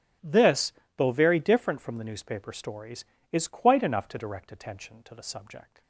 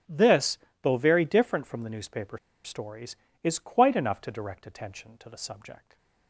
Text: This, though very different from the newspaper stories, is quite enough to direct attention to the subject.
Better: first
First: starts louder than the rest; strong; until 1.4 s; 11 dB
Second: starts louder than the rest; strong; until 1.3 s; 11 dB // pauses between "newspaper" and "stories"; slight; at 2.3 s; 0.27 s long // stays silent after the last word; slight; from 5.7 s on; 0.5 s long

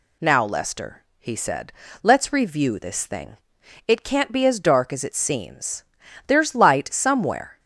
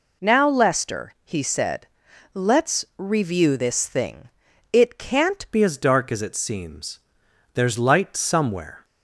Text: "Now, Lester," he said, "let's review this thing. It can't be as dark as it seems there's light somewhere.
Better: first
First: pauses between "seems" and "there's"; at 5.8 s; 0.44 s long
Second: changes voice at "be"; from 5.5 s on; 3.3 s long // pauses between "seems" and "there's"; noticeable; at 7.0 s; 0.54 s long

